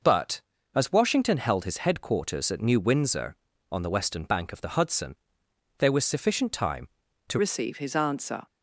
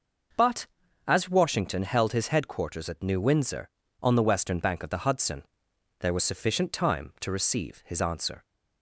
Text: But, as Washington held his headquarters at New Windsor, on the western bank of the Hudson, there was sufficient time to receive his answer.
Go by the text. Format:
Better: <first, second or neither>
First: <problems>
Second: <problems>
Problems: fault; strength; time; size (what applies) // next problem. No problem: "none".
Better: second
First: changes voice at "receive"; from 7.3 s on; 1.1 s long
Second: none